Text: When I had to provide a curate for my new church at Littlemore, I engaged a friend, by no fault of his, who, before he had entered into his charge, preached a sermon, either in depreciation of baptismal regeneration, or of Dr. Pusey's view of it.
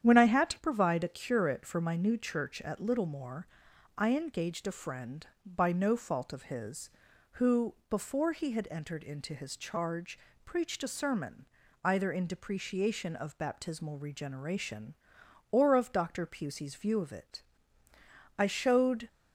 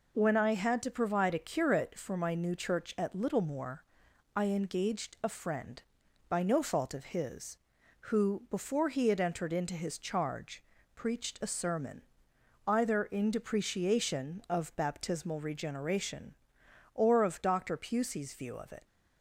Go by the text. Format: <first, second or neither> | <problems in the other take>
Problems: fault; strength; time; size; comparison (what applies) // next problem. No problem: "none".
second | starts louder than the rest; strong; until 1.0 s; 9 dB // goes on to say "I showed"; noticeable; from 18.3 s on; 0.70 s long